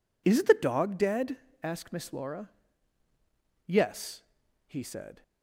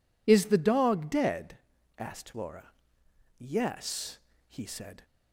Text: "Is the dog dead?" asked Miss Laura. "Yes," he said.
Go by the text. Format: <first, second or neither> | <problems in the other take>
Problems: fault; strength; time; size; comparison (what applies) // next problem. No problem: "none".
first | skips "Miss"; at 2.3 s